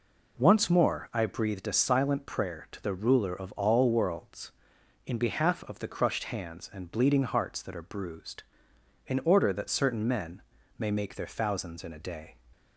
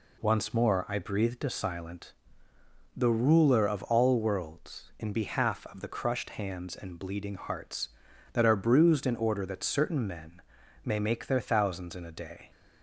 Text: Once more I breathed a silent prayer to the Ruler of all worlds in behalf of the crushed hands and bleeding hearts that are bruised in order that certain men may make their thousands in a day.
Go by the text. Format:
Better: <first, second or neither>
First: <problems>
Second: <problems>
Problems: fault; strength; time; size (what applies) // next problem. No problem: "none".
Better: first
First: pauses between "men" and "may"; slight; at 10.4 s; 0.34 s long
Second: skips "prayer to"; at 2.5 s // pauses between "men" and "may"; at 10.4 s; 0.42 s long